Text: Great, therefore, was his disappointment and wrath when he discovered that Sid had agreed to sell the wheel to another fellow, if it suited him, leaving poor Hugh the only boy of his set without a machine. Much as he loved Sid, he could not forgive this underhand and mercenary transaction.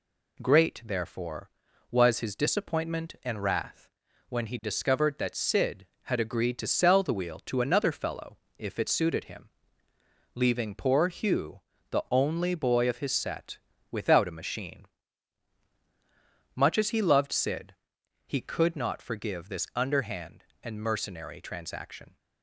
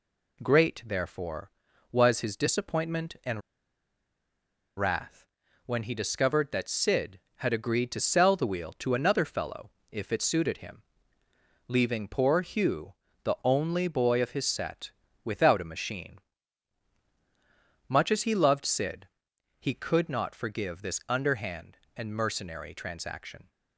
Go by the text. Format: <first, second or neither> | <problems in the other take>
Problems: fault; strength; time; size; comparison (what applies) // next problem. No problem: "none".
first | pauses between "and" and "wrath"; strong; at 3.4 s; 1.3 s long // pauses between "wrath" and "when"; at 5.2 s; 0.40 s long; also in the first // pauses between "Hugh" and "the"; slight; at 12.9 s; 0.30 s long; slight in the first // pauses between "set" and "without"; slight; at 14.9 s; 0.34 s long; slight in the first